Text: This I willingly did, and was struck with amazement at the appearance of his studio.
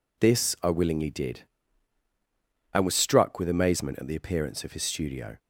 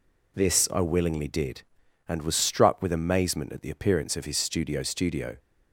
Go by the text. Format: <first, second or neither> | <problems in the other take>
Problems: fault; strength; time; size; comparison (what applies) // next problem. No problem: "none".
first | says "studio" twice; at 4.8 s